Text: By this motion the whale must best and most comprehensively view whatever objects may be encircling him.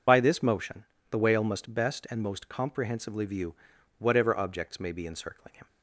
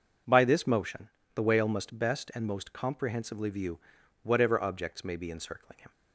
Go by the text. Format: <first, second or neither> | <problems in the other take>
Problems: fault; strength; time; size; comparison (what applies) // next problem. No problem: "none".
second | loses the start of "By"; at 0.0 s; 55 ms // pauses between "motion" and "the"; slight; at 0.8 s; 0.26 s long; slight in the second // pauses between "view" and "whatever"; at 3.5 s; 0.44 s long; also in the second